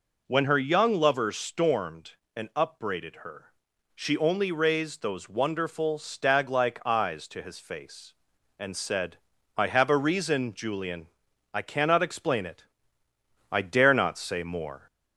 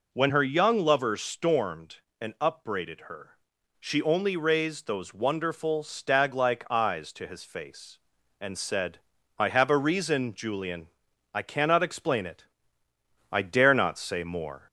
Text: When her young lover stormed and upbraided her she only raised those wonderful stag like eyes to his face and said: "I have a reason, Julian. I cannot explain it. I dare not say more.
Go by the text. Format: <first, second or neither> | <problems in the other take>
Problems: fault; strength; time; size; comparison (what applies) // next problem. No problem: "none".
neither | pauses between "her" and "she"; noticeable; the same in both